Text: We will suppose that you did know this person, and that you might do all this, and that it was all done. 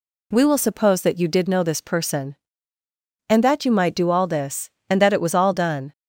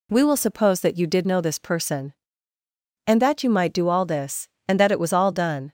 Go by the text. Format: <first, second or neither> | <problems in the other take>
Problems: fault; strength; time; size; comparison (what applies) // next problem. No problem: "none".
neither | none